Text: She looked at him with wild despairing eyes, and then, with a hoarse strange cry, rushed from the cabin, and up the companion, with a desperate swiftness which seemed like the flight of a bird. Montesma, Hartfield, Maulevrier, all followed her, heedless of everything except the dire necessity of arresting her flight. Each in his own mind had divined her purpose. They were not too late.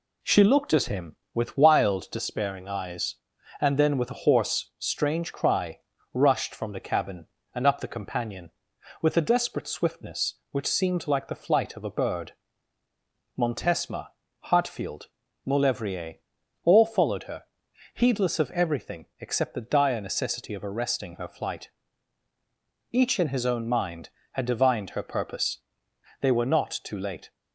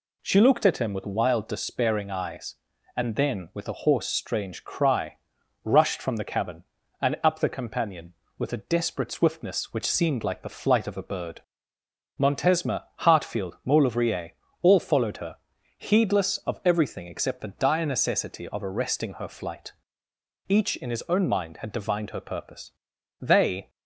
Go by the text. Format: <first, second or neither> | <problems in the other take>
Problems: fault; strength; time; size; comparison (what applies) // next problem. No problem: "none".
first | stops before "were not too late"; at 23.6 s